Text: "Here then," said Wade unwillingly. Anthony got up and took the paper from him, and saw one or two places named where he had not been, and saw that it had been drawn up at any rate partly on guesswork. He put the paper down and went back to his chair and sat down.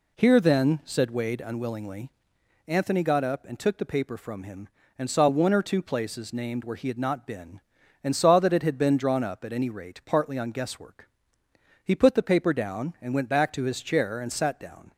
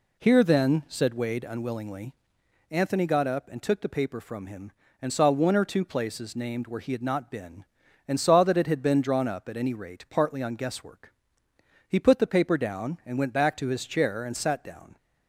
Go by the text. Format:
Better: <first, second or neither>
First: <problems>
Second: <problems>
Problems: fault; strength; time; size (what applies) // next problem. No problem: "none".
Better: neither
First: none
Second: none